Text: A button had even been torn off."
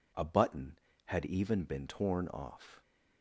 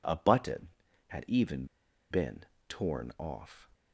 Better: first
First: none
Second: pauses between "even" and "been"; noticeable; at 1.6 s; 0.46 s long // pauses between "been" and "torn"; slight; at 2.4 s; 0.26 s long

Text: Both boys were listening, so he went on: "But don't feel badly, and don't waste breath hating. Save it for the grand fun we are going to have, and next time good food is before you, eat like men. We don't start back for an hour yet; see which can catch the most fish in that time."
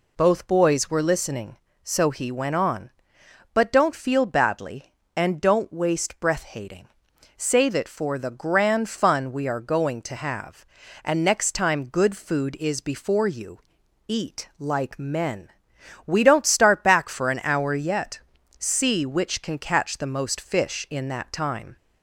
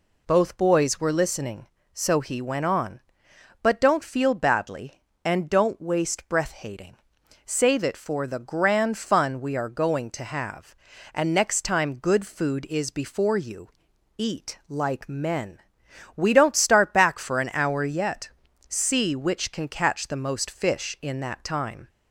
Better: neither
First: none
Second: none

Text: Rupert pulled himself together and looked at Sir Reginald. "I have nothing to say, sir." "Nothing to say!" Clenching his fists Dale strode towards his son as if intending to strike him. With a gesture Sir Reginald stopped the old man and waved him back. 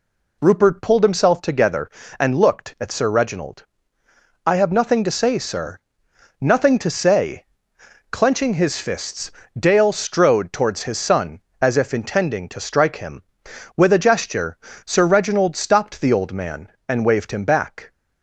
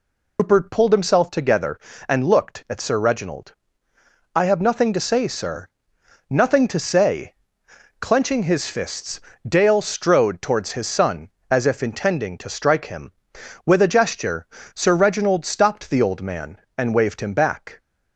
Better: first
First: pauses between "fists" and "Dale"; slight; at 9.3 s; 0.26 s long // pauses between "gesture" and "Sir"; slight; at 14.5 s; 0.30 s long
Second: loses the start of "Rupert"; at 0.3 s; 105 ms // pauses between "fists" and "Dale"; slight; at 9.2 s; 0.26 s long // pauses between "gesture" and "Sir"; slight; at 14.4 s; 0.30 s long

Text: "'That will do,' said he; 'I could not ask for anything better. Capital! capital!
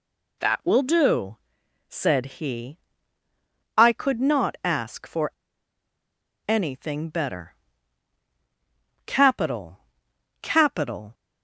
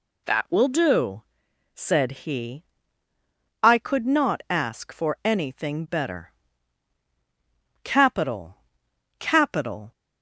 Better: second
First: pauses between "for" and "anything"; at 5.3 s; 1.1 s long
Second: none

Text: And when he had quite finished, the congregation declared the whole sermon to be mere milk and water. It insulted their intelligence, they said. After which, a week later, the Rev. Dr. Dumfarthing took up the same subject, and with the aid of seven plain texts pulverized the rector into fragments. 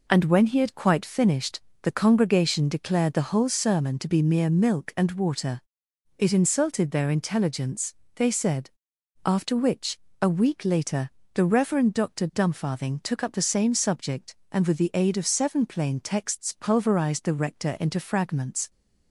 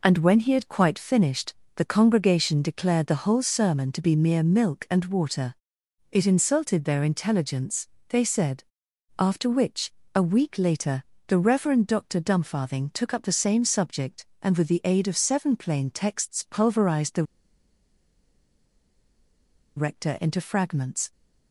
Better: first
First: none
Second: pauses between "the" and "rector"; strong; at 17.2 s; 2.5 s long

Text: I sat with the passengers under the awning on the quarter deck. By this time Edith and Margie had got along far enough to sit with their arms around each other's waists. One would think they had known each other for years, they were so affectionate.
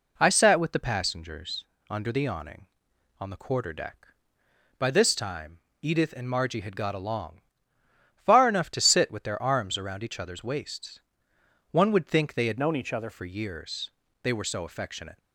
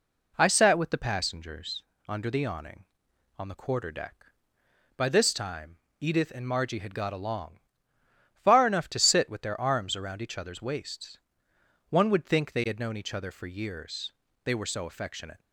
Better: second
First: pauses between "passengers" and "under"; slight; at 1.6 s; 0.24 s long // pauses between "time" and "Edith"; slight; at 5.5 s; 0.24 s long // pauses between "along" and "far"; noticeable; at 7.4 s; 0.74 s long // changes voice from "known" to "other"; from 12.5 to 13.0 s; 0.5 s long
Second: pauses between "passengers" and "under"; slight; at 1.8 s; 0.24 s long // pauses between "time" and "Edith"; slight; at 5.7 s; 0.24 s long // pauses between "along" and "far"; noticeable; at 7.5 s; 0.74 s long

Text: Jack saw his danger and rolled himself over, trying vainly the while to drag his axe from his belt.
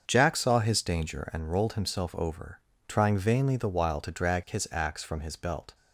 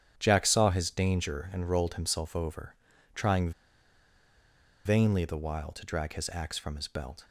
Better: first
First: starts louder than the rest; until 1.0 s; 6.5 dB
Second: starts louder than the rest; strong; until 1.1 s; 10 dB // pauses between "trying" and "vainly"; strong; at 3.5 s; 1.3 s long

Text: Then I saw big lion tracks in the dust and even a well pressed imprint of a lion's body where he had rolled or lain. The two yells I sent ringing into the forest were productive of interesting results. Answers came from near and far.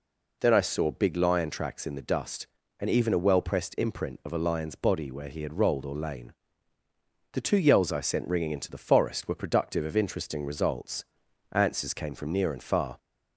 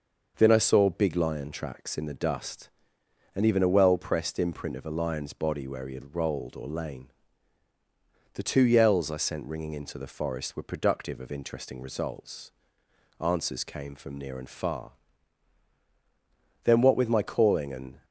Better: first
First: none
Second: starts louder than the rest; noticeable; until 1.3 s; 6 dB // goes on to say "Then what with my calling and"; from 16.6 s on; 1.4 s long

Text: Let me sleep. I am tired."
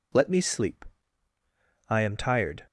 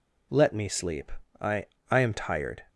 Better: first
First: none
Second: says "I" twice; at 1.8 s

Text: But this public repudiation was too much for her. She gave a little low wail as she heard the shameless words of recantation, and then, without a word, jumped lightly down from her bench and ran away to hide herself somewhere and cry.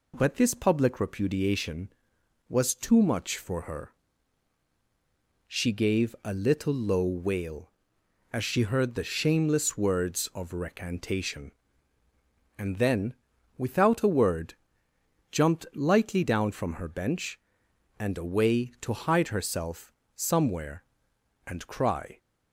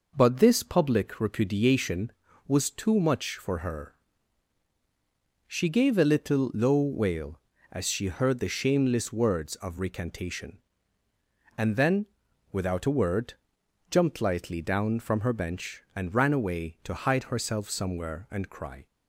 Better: second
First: skips "ran"; at 18.1 s // pauses between "herself" and "somewhere"; slight; at 19.9 s; 0.22 s long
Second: none

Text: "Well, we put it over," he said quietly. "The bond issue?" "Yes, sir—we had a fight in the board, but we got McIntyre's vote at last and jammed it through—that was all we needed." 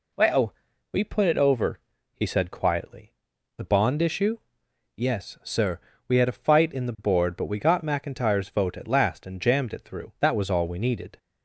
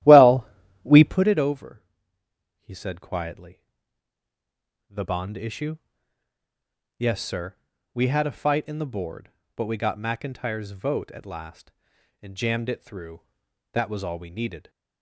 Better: first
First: none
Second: starts louder than the rest; strong; until 1.2 s; 13.5 dB

